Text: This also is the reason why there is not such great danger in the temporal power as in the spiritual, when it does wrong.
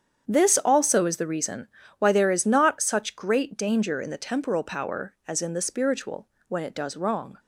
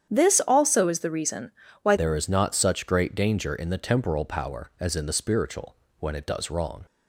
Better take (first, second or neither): first